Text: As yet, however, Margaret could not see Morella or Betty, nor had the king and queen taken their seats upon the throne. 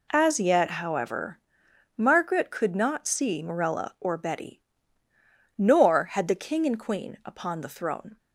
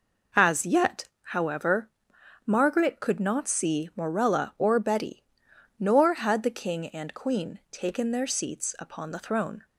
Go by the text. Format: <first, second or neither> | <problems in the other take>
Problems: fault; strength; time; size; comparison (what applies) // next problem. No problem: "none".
second | skips "taken their seats"; at 7.2 s